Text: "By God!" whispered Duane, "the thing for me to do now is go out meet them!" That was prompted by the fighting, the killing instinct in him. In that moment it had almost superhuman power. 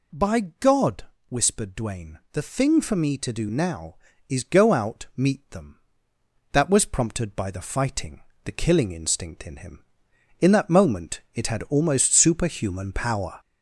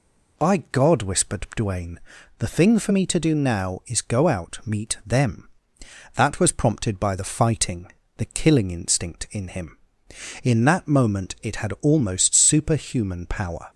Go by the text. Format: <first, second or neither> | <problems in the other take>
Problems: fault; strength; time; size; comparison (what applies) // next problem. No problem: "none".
second | gets louder; throughout; 3.5 dB // pauses between "By" and "God"; slight; at 0.4 s; 0.20 s long